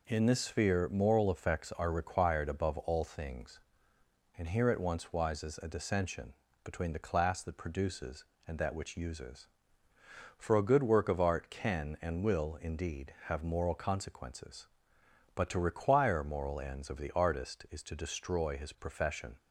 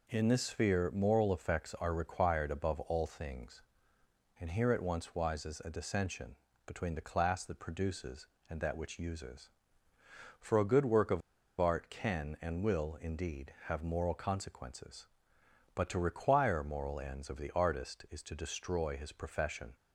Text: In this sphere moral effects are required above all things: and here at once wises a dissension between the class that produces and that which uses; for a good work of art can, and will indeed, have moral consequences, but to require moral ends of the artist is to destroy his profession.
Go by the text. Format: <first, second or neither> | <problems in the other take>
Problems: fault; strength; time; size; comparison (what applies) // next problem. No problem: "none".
first | pauses between "dissension" and "between"; slight; at 6.3 s; 0.28 s long; slight in the first // pauses between "of" and "art"; at 11.2 s; 0.39 s long